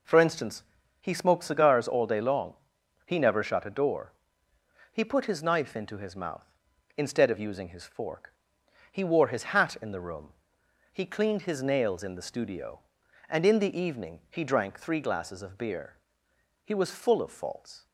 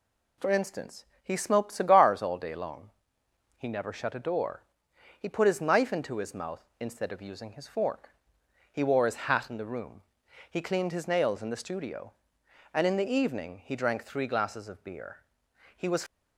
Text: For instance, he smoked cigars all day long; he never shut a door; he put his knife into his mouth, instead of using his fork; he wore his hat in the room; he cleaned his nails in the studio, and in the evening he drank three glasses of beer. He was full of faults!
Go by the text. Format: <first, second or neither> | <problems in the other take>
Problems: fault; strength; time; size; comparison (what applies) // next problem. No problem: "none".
first | stops before "full of faults"; at 16.0 s